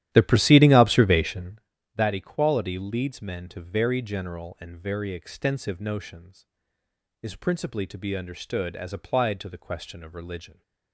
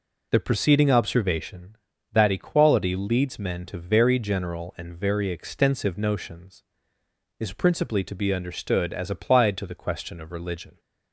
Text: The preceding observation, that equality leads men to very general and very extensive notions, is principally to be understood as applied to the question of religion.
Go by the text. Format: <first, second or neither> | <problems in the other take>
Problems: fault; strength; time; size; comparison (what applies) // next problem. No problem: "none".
second | starts louder than the rest; strong; until 1.7 s; 12.5 dB